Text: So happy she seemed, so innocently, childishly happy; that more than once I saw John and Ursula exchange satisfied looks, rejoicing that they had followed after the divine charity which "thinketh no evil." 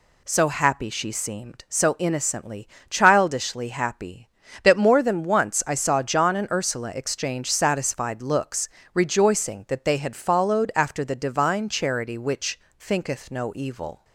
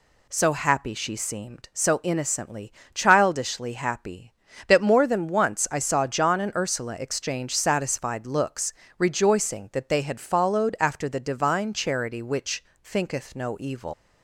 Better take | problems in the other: first | pauses between "which" and "thinketh"; slight; at 12.6 s; 0.20 s long; slight in the first // leaves "evil" unfinished; at 13.9 s; 150 ms

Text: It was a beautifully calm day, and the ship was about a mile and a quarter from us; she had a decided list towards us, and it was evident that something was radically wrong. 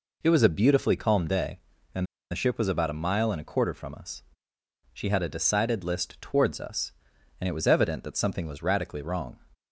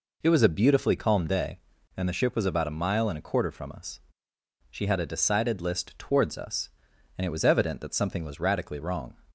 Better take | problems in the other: second | pauses between "and" and "the"; slight; at 2.0 s; 0.26 s long

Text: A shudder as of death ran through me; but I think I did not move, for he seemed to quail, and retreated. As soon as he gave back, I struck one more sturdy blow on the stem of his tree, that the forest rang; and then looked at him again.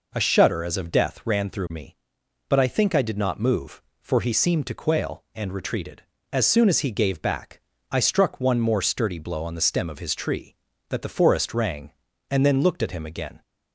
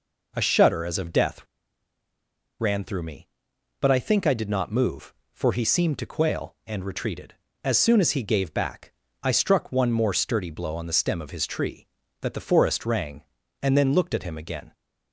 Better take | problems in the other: first | pauses between "death" and "ran"; at 1.4 s; 1.1 s long

